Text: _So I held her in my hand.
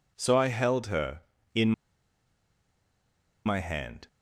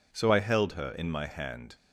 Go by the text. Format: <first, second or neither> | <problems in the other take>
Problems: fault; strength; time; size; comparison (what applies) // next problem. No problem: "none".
second | pauses between "in" and "my"; strong; at 1.7 s; 1.7 s long